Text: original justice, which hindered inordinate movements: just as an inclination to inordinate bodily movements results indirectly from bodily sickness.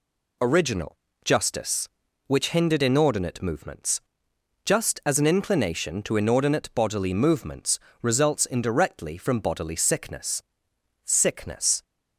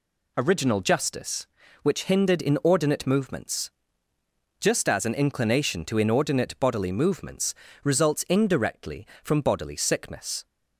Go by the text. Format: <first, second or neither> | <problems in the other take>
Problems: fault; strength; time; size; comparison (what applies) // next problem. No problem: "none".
second | pauses between "original" and "justice"; slight; at 0.9 s; 0.28 s long // pauses between "movements" and "results"; slight; at 7.8 s; 0.22 s long; slight in the second // says "sickness" twice; at 11.0 s